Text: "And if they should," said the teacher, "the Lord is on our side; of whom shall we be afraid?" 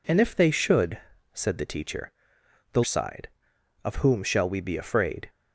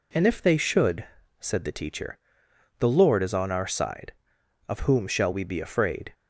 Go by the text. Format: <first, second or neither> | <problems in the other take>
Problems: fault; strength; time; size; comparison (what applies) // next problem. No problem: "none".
second | skips "Lord is on our"; at 2.8 s